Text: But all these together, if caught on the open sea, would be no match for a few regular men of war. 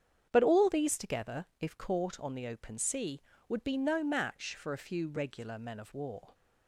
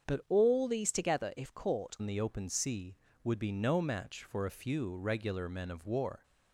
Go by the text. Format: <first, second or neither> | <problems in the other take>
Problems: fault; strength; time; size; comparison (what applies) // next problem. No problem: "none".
first | starts louder than the rest; strong; until 1.1 s; 7.5 dB; strong in the first // changes voice at "on"; from 1.9 s on; 4.3 s long